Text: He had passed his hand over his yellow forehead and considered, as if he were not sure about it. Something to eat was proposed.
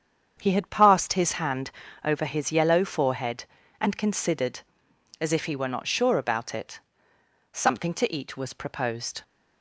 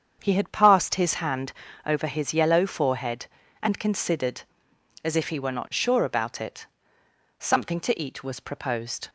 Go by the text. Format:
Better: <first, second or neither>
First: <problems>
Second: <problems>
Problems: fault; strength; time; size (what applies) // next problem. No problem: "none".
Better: neither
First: starts louder than the rest; strong; until 1.4 s; 7.5 dB // pauses between "hand" and "over"; slight; at 1.7 s; 0.32 s long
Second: starts louder than the rest; strong; until 1.2 s; 7.5 dB // pauses between "hand" and "over"; slight; at 1.5 s; 0.32 s long